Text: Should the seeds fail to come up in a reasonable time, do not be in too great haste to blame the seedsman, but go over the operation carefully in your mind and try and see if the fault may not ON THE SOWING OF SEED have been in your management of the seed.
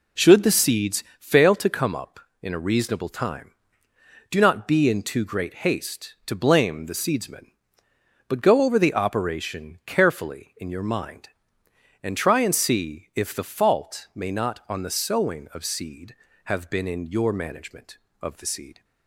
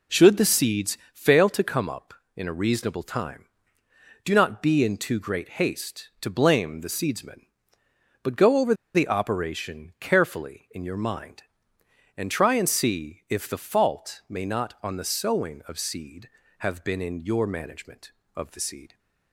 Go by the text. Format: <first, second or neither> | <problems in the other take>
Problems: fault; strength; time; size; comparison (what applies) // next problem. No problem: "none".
first | pauses between "seeds" and "fail"; slight; at 0.9 s; 0.16 s long; slight in the first // pauses between "over" and "the"; slight; at 8.7 s; 0.21 s long